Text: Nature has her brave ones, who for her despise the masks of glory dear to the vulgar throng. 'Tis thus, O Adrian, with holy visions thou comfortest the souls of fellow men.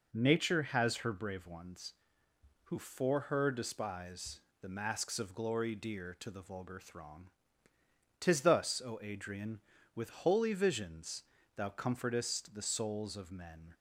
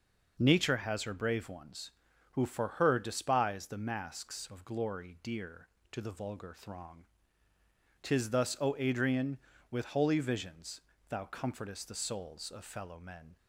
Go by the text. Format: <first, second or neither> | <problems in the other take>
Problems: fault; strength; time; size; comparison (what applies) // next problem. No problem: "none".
second | pauses between "despise" and "the"; slight; at 4.4 s; 0.20 s long // pauses between "visions" and "thou"; slight; at 11.2 s; 0.34 s long; slight in the second // skips "fellow"; at 13.3 s